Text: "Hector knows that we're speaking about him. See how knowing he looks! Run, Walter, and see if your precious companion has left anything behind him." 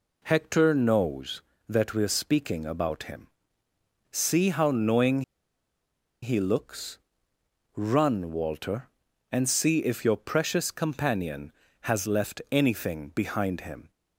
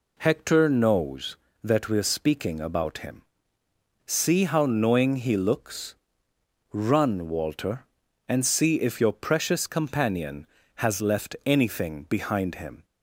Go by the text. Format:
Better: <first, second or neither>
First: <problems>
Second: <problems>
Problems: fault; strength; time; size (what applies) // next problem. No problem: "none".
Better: second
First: pauses between "knowing" and "he"; at 5.2 s; 1.0 s long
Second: none